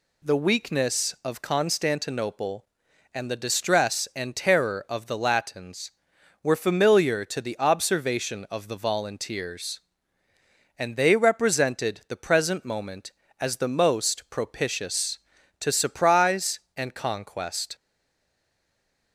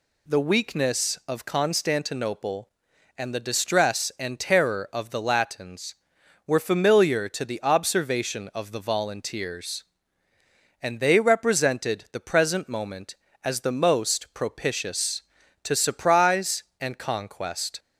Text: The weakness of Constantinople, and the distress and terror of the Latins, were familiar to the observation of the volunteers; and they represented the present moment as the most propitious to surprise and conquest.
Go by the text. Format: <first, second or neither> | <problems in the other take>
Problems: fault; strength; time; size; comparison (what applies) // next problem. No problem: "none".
second | stays silent after the last word; noticeable; from 17.7 s on; 1.4 s long